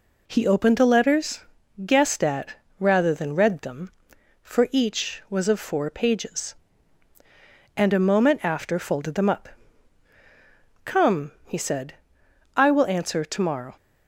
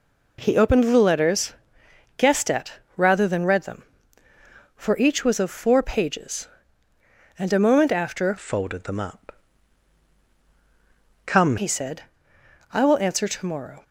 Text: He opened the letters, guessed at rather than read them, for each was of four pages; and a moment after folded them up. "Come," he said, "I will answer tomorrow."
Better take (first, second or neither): first